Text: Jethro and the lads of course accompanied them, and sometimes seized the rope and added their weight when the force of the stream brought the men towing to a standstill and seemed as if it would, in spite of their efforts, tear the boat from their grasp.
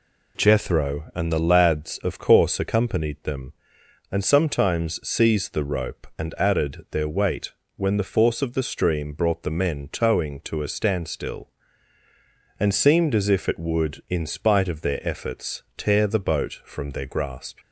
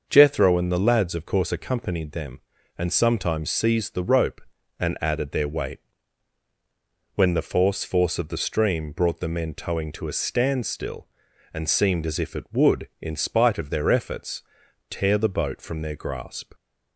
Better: first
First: pauses between "weight" and "when"; slight; at 7.5 s; 0.24 s long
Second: starts louder than the rest; until 1.0 s; 6.5 dB // pauses between "weight" and "when"; strong; at 5.7 s; 1.3 s long // says "force" twice; at 7.8 s

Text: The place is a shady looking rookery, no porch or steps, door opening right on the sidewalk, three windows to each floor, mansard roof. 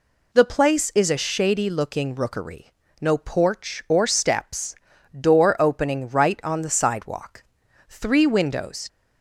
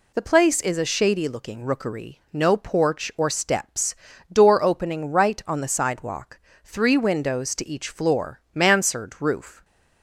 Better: second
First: stops before "to each floor mansard roof"; at 8.8 s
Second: none

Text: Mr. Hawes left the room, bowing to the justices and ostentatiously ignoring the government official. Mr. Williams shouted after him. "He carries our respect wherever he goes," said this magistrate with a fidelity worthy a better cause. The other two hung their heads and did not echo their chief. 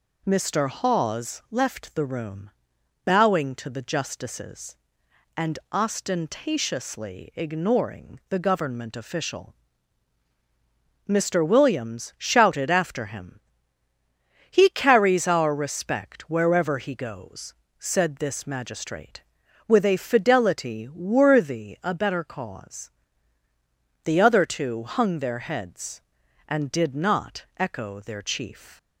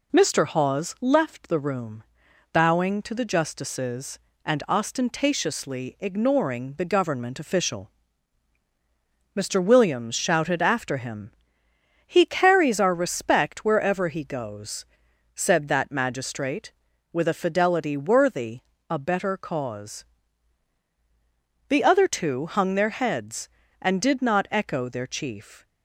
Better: first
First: none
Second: says "that" for "this"; at 15.6 s // pauses between "worthy" and "a"; slight; at 18.6 s; 0.28 s long

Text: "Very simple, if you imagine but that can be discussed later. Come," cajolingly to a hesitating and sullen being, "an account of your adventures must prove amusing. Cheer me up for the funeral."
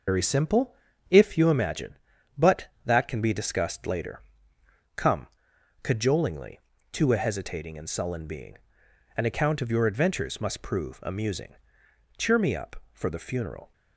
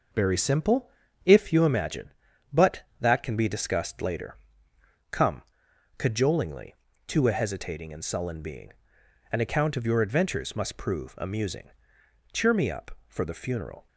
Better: second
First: loses the start of "Very"; at 0.0 s; 95 ms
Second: none

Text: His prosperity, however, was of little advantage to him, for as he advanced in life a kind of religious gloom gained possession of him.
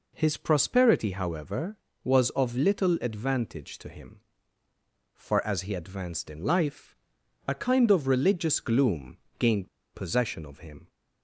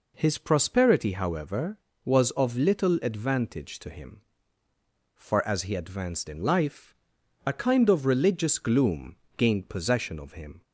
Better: second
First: pauses between "life" and "a"; noticeable; at 6.9 s; 0.54 s long // pauses between "gloom" and "gained"; slight; at 9.1 s; 0.22 s long // pauses between "gained" and "possession"; slight; at 9.6 s; 0.26 s long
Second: pauses between "life" and "a"; noticeable; at 6.9 s; 0.53 s long // pauses between "gloom" and "gained"; slight; at 9.1 s; 0.22 s long

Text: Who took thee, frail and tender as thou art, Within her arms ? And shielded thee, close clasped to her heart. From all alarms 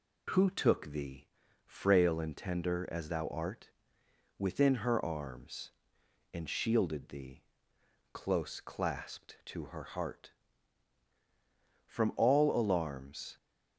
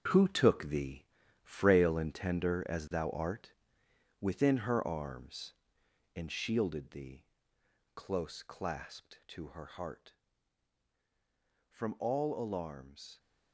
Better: first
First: none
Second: gets quieter; strong; throughout; 10 dB

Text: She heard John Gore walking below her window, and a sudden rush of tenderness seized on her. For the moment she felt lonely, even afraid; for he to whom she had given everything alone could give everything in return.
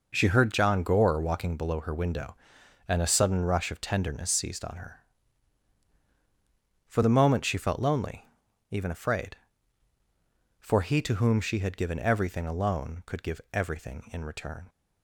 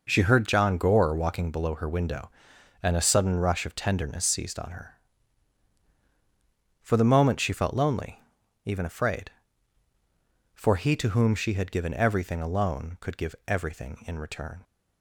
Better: neither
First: none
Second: none

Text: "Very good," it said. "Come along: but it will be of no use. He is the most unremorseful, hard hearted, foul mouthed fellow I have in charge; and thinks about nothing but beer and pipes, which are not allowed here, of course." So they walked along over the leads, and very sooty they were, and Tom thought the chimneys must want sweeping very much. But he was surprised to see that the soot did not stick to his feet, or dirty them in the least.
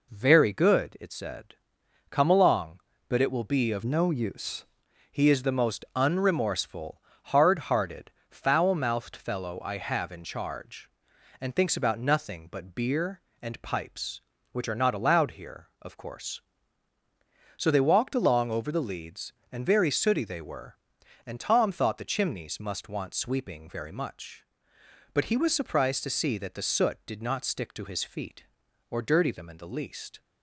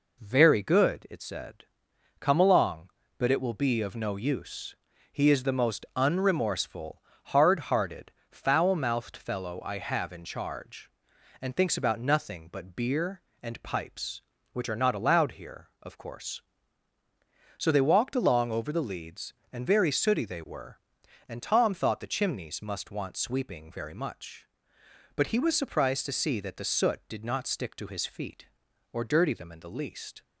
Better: second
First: changes voice from "no" to "use"; from 3.8 to 4.6 s; 0.8 s long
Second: none

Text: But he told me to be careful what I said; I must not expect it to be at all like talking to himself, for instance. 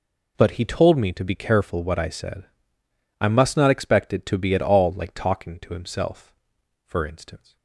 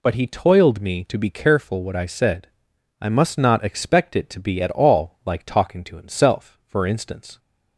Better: first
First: none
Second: says "toiled" for "told"; at 0.2 s

